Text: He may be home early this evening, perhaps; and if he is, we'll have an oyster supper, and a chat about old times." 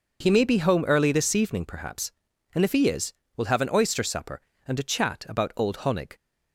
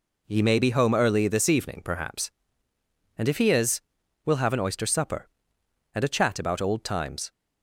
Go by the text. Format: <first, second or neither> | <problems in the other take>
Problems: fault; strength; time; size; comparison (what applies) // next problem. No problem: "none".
second | says "honig" for "times"; at 5.7 s